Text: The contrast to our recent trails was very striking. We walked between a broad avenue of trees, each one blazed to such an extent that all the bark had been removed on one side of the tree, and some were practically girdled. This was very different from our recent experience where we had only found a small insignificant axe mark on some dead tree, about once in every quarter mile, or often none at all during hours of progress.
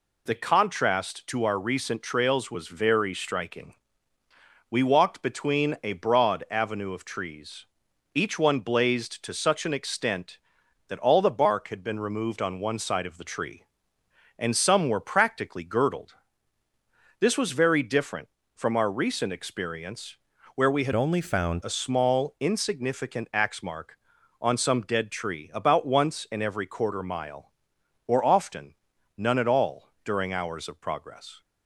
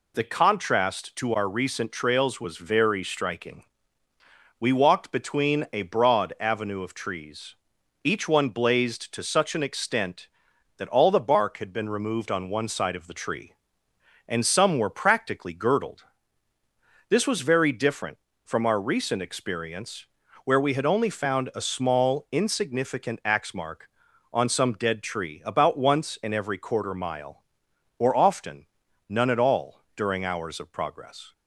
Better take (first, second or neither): second